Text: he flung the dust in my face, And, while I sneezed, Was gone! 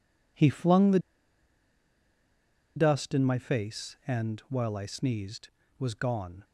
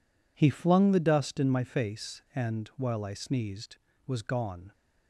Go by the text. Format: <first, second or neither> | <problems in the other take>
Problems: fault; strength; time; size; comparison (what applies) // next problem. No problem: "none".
second | pauses between "the" and "dust"; strong; at 0.9 s; 1.7 s long